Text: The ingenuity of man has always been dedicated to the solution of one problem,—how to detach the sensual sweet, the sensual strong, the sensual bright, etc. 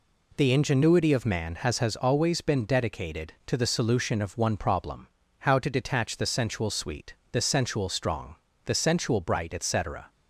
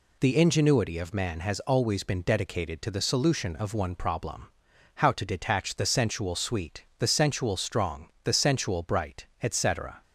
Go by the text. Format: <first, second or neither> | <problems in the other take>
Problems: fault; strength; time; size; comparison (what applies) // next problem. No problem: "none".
second | says "has" twice; at 1.7 s